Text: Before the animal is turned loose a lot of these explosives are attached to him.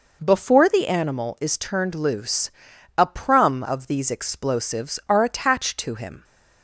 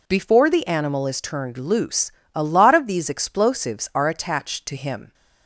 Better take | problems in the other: second | pauses between "loose" and "a"; noticeable; at 2.5 s; 0.46 s long; slight in the second // says "prum" for "lot"; at 3.0 s

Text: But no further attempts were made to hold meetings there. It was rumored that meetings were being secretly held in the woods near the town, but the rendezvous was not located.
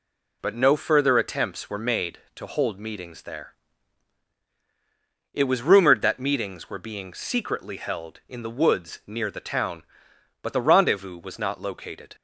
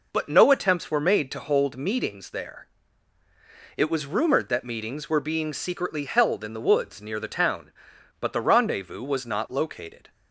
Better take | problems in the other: first | skips "further"; at 0.5 s

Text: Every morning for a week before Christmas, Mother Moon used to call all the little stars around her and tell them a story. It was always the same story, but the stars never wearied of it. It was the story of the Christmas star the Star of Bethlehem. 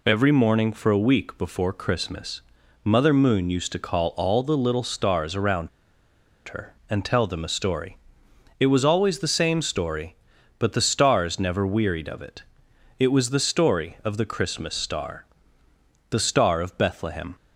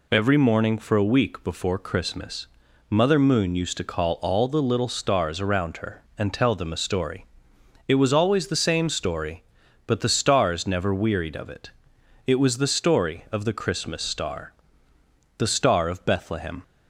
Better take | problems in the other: second | pauses between "around" and "her"; noticeable; at 5.6 s; 0.79 s long // pauses between "star" and "the"; noticeable; at 15.2 s; 0.86 s long; noticeable in the second

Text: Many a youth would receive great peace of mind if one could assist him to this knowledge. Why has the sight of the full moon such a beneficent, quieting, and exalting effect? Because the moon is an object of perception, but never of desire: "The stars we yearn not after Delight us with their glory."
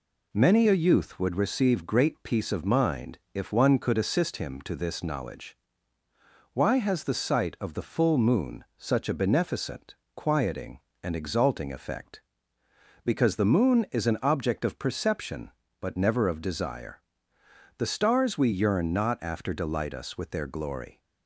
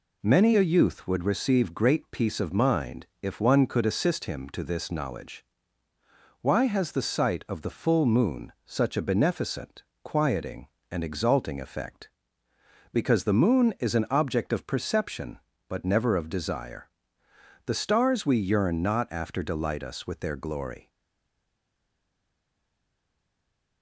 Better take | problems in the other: first | pauses between "mind" and "if"; slight; at 3.0 s; 0.16 s long; slight in the first // stays silent after the last word; strong; from 20.8 s on; 3.0 s long

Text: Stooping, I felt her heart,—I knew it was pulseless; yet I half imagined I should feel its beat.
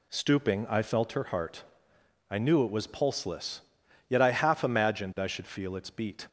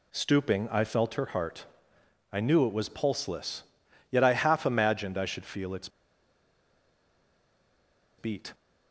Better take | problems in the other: first | pauses between "its" and "beat"; strong; at 5.8 s; 2.2 s long

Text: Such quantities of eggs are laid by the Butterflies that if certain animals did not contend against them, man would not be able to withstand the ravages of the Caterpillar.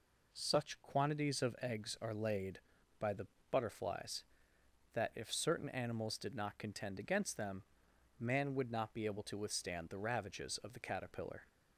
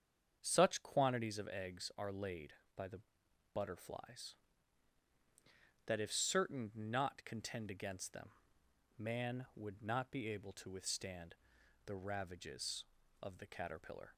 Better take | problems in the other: first | starts louder than the rest; strong; until 1.4 s; 7.5 dB // pauses between "the" and "Butterflies"; noticeable; at 3.0 s; 0.52 s long; slight in the first // skips "animals did"; at 6.7 s // pauses between "withstand" and "the"; noticeable; at 11.3 s; 0.54 s long

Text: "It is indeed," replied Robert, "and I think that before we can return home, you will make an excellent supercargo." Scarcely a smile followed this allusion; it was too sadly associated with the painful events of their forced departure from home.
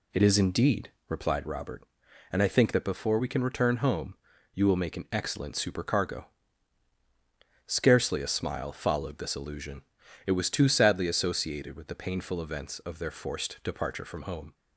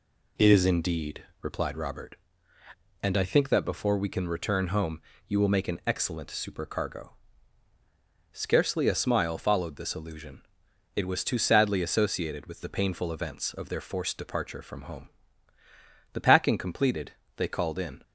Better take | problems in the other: first | goes on to say "The packing completed they called in"; strong; from 16.1 s on; 1.8 s long

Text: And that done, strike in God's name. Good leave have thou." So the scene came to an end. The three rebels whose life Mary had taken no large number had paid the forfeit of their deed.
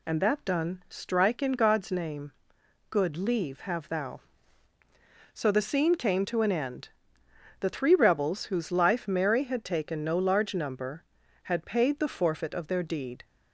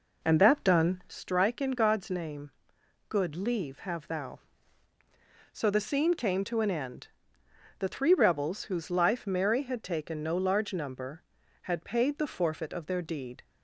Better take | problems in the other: first | starts louder than the rest; noticeable; until 1.1 s; 4 dB

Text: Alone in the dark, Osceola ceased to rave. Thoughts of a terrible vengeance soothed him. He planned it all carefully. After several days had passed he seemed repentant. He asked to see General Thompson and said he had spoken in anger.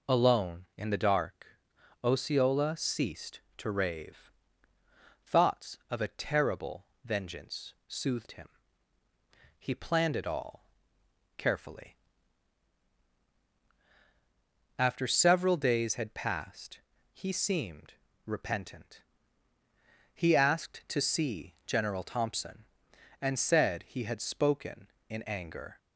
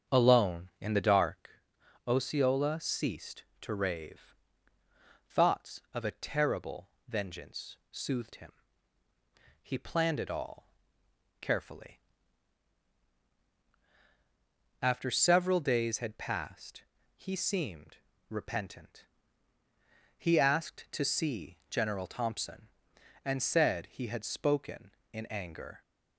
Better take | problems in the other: first | starts louder than the rest; strong; until 1.5 s; 7 dB // pauses between "terrible" and "vengeance"; slight; at 6.8 s; 0.22 s long; slight in the first // pauses between "vengeance" and "soothed"; slight; at 7.7 s; 0.16 s long; slight in the first // pauses between "all" and "carefully"; noticeable; at 10.6 s; 0.72 s long; noticeable in the first // pauses between "passed" and "he"; slight; at 16.8 s; 0.34 s long; slight in the first // pauses between "seemed" and "repentant"; slight; at 17.9 s; 0.32 s long; slight in the first

